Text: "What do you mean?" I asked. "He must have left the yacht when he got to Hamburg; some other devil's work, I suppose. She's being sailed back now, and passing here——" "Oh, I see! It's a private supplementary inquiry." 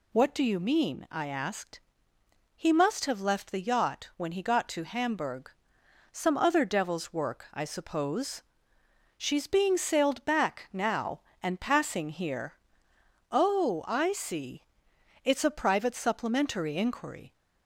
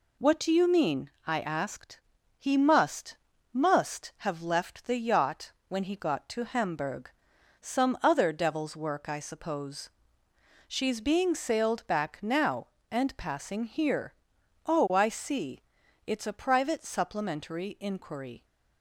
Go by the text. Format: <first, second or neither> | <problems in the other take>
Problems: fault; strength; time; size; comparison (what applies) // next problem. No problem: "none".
first | says "must" twice; at 3.5 s // pauses between "yacht" and "when"; slight; at 5.5 s; 0.16 s long